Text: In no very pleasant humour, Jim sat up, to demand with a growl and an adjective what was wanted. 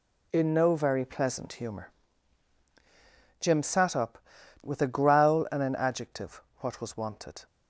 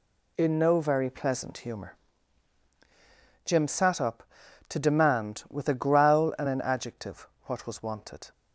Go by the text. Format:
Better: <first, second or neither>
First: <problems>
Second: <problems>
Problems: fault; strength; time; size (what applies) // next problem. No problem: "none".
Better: second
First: skips "to demand"; at 4.3 s // pauses between "adjective" and "what"; slight; at 6.4 s; 0.16 s long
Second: pauses between "adjective" and "what"; slight; at 7.2 s; 0.16 s long